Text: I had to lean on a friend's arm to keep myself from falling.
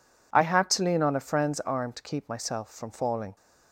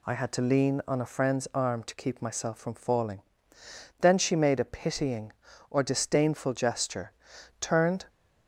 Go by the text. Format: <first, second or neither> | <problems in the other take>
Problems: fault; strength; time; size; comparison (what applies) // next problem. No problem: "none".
first | goes on to say "Then she made a pitying or disdainful gesture turned"; strong; from 3.9 s on; 4.0 s long